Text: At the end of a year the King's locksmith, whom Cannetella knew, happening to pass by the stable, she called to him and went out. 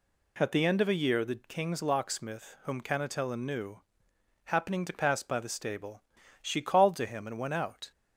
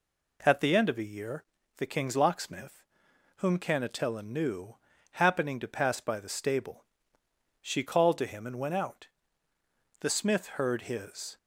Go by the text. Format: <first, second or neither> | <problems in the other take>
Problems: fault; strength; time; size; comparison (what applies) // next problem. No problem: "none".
first | pauses between "year" and "the"; slight; at 1.4 s; 0.34 s long // goes on to say "The smith heard his"; from 9.9 s on; 1.3 s long